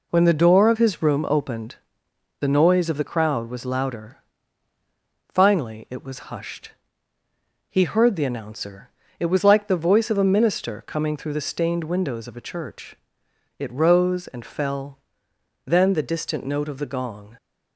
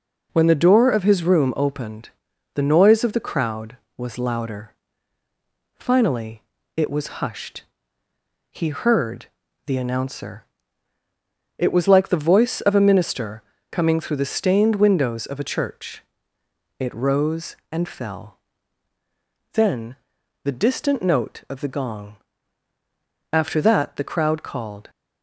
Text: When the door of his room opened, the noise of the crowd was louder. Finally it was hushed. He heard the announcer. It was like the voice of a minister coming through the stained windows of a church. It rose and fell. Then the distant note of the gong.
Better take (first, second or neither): first